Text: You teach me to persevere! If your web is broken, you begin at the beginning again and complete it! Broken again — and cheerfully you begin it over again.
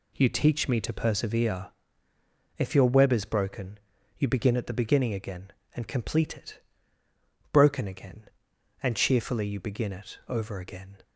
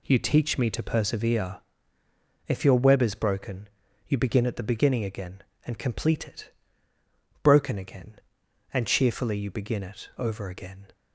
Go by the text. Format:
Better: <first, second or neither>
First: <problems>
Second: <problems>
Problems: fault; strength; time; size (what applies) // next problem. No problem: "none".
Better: neither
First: none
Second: none